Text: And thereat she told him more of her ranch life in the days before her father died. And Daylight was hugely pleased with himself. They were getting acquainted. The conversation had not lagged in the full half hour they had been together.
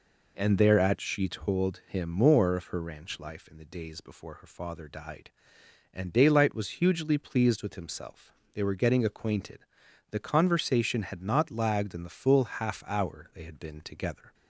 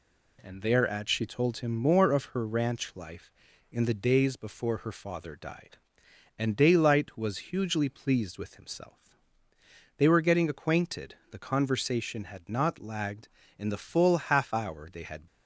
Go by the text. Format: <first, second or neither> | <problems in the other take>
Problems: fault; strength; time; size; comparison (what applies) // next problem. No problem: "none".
first | stops before "been together"; at 15.2 s